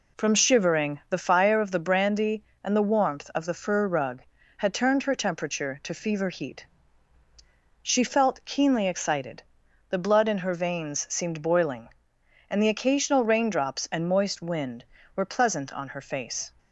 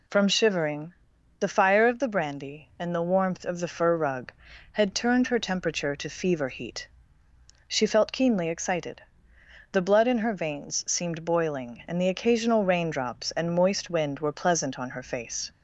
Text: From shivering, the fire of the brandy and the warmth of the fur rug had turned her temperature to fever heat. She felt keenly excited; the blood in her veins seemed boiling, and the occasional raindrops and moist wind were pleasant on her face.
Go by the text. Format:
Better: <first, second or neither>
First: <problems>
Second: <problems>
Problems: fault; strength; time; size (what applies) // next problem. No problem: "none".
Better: neither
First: none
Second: none